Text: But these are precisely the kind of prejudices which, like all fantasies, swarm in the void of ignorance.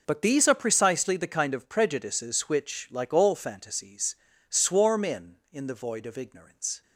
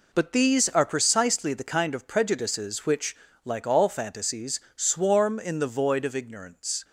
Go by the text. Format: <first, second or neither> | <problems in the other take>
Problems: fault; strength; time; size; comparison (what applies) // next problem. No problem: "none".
second | says "in" twice; at 5.5 s